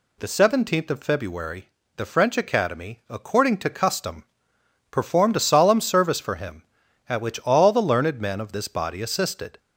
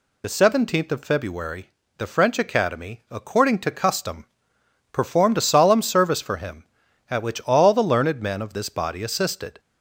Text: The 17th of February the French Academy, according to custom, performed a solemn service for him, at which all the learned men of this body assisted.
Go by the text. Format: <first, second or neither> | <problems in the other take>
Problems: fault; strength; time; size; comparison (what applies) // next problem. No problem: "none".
first | loses the start of "The"; at 0.2 s; 25 ms // pauses between "February" and "the"; slight; at 1.6 s; 0.26 s long; slight in the first